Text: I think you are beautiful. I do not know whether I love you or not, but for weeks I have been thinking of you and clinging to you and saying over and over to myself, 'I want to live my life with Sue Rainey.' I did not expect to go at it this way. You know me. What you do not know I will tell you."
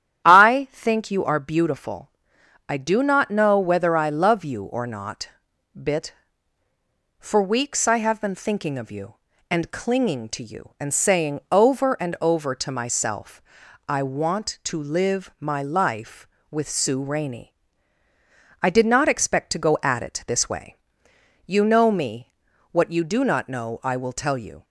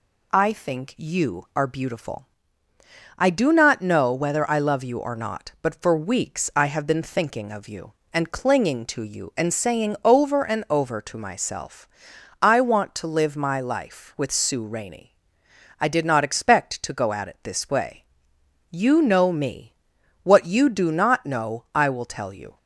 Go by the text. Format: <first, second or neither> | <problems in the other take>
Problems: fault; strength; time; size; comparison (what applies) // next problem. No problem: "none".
second | starts louder than the rest; strong; until 1.3 s; 10.5 dB // says "bit" for "but"; at 5.8 s